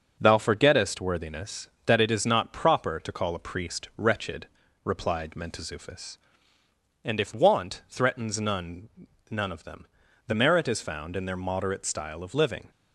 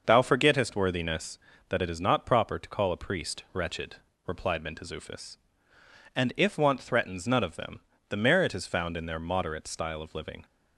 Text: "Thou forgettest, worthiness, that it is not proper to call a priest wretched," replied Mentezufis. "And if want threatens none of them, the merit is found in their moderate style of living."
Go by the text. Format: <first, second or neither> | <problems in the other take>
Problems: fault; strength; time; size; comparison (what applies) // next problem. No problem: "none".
second | starts louder than the rest; noticeable; until 1.2 s; 6 dB // says "none" twice; at 9.2 s